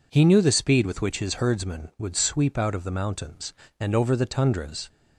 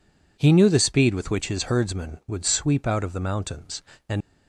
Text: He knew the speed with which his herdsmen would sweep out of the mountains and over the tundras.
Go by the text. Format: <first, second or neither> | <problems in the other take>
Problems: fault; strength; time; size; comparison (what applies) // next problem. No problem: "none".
first | stops before "over the tundras"; at 4.2 s